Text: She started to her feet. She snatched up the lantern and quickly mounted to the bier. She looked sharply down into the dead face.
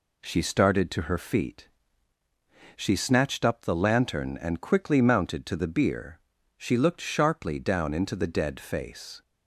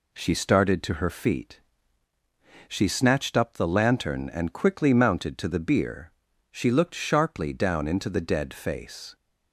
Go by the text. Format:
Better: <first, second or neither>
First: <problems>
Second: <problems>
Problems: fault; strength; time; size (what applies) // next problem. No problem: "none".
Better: neither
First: none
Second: none